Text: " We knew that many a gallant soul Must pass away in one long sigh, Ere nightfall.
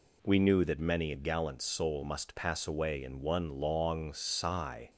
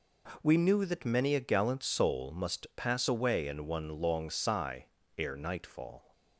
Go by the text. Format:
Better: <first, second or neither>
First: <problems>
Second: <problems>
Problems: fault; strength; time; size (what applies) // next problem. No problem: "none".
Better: second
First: stops before "Ere nightfall"; at 4.8 s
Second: none